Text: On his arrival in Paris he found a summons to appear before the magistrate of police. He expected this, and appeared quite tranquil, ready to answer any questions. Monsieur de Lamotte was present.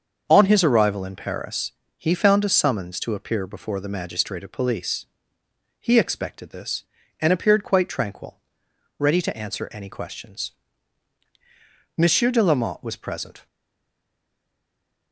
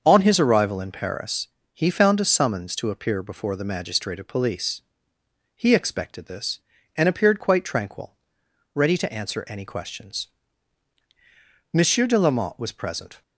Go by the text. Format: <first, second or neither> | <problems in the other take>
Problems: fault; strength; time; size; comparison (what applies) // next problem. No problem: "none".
second | starts louder than the rest; until 1.2 s; 6.5 dB; also in the second // pauses between "Paris" and "he"; slight; at 1.7 s; 0.26 s long; slight in the second // stays silent after the last word; noticeable; from 13.4 s on; 1.7 s long